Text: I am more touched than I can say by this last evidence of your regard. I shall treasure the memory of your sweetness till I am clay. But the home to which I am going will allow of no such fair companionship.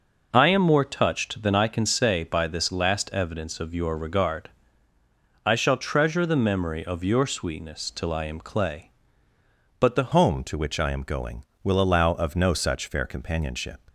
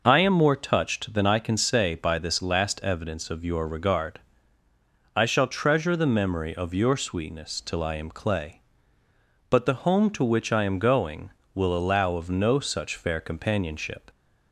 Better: second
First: changes voice at "home"; from 10.1 s on; 3.7 s long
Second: none

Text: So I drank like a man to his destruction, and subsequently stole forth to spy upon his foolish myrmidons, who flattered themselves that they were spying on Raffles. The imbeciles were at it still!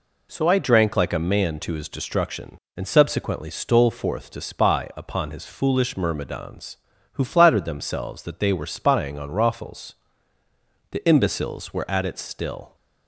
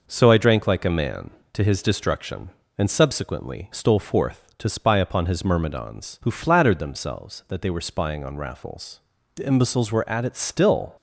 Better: first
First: none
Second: skips "foolish"; at 5.4 s

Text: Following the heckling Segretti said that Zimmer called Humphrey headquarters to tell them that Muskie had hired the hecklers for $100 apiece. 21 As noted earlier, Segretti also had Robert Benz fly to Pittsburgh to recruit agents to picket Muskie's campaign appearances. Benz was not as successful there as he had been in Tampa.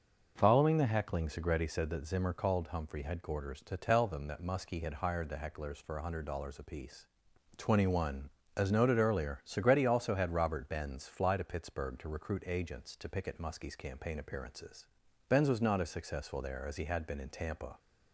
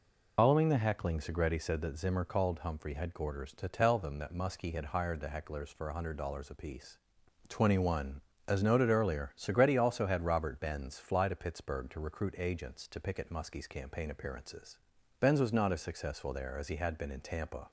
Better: first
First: none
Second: loses the start of "Following"; at 0.3 s; 115 ms

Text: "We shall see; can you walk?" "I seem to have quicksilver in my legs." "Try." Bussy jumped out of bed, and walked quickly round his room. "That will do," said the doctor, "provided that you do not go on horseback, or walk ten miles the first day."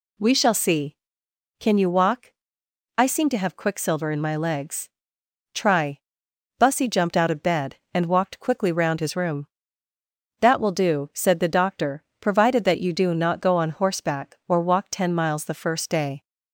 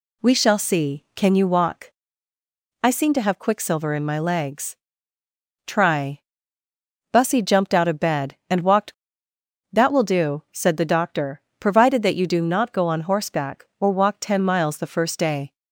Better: first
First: none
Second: skips "quickly round his room"; at 9.3 s

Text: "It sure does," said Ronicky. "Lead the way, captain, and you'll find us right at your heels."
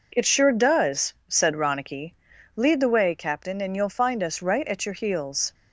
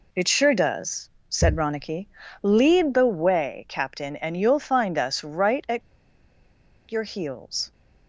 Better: first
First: none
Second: pauses between "at" and "your"; at 5.8 s; 1.1 s long

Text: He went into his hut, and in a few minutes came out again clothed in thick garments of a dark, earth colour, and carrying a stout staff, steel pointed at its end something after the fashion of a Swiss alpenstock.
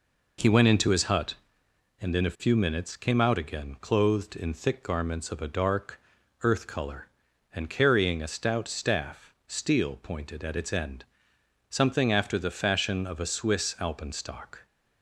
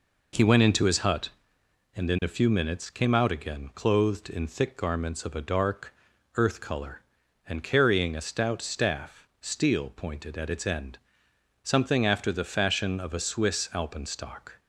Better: neither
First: pauses between "end" and "something"; noticeable; at 11.0 s; 0.64 s long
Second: pauses between "end" and "something"; noticeable; at 10.9 s; 0.64 s long

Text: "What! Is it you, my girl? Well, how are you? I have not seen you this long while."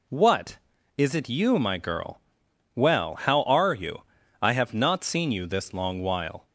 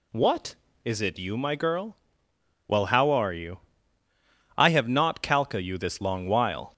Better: first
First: none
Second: says "calca" for "seen"; at 5.2 s

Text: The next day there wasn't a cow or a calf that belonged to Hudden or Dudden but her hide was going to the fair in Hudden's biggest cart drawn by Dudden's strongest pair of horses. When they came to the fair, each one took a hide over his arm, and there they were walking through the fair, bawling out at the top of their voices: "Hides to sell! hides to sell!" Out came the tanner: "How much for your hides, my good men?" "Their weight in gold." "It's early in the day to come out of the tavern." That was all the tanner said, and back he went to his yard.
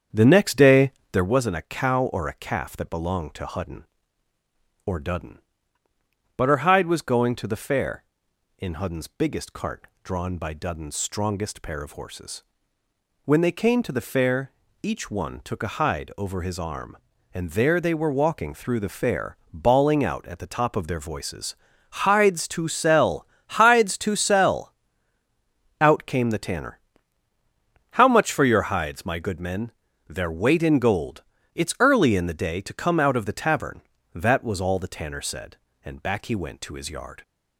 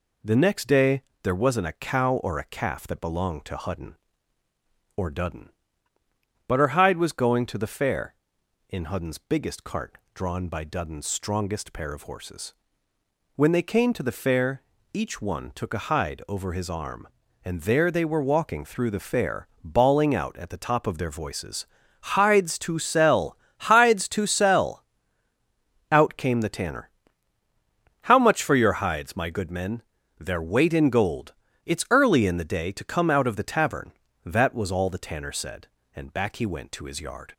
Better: second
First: starts louder than the rest; strong; until 1.4 s; 7.5 dB // pauses between "day" and "there"; slight; at 0.9 s; 0.22 s long // pauses between "cart" and "drawn"; slight; at 9.8 s; 0.16 s long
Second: pauses between "day" and "there"; slight; at 1.0 s; 0.22 s long // pauses between "cart" and "drawn"; slight; at 9.9 s; 0.16 s long

